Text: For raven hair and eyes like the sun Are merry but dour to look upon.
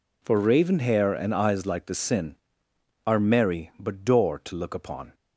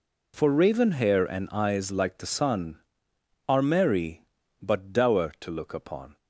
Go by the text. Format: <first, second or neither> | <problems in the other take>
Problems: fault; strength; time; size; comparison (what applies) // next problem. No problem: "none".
second | says "sin" for "sun"; at 1.9 s